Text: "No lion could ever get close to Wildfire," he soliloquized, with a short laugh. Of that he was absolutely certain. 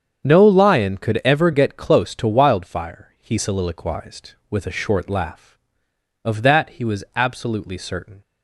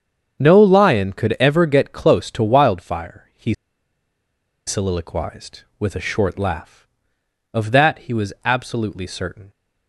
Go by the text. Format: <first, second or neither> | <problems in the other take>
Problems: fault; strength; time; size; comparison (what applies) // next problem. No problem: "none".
first | starts louder than the rest; strong; until 1.4 s; 7.5 dB; strong in the first // pauses between "he" and "soliloquized"; at 3.5 s; 1.1 s long